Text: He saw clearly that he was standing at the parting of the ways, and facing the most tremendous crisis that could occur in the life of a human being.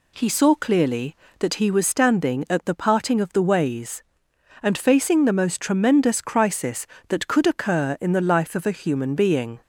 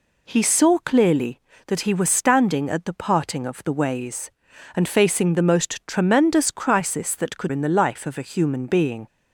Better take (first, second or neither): first